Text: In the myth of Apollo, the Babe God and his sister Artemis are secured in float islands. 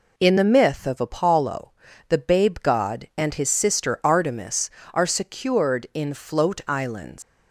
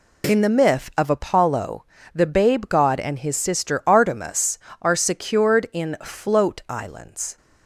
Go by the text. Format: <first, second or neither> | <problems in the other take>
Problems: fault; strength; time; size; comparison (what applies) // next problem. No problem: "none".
second | leaves "islands" unfinished; at 7.2 s; 115 ms